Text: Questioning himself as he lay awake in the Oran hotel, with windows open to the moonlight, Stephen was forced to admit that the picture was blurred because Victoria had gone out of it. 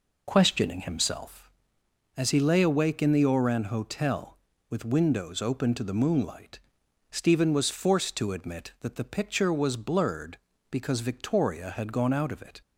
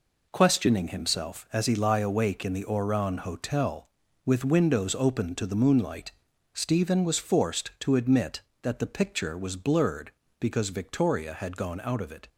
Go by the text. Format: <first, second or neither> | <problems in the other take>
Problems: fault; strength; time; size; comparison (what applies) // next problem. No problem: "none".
first | says "lie" for "lay"; at 1.7 s